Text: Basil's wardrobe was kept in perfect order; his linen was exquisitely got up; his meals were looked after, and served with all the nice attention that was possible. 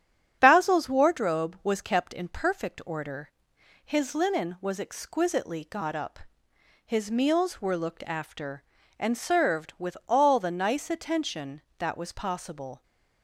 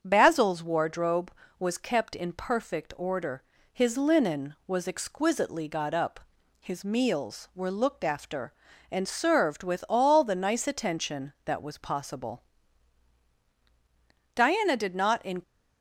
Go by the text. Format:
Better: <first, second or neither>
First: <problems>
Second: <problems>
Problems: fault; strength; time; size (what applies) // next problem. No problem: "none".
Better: first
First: starts louder than the rest; strong; until 1.4 s; 8.5 dB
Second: starts louder than the rest; strong; until 1.0 s; 7 dB // goes on to say "Diana did not in"; noticeable; from 14.3 s on; 1.0 s long